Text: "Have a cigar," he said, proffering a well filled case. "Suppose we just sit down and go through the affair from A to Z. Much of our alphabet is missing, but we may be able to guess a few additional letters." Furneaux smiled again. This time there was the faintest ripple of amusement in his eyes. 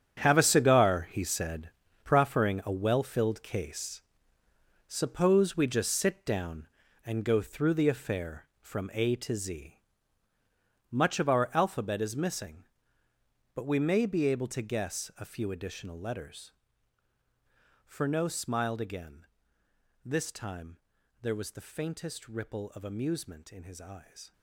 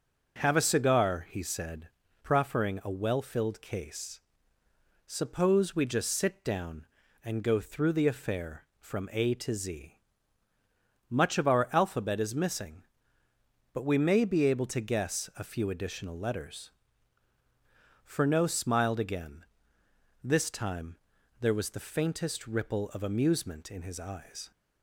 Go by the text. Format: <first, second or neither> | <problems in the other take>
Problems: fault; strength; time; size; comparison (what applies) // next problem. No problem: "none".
second | gets quieter; strong; throughout; 13 dB // pauses between "time" and "there"; at 20.8 s; 0.42 s long; also in the second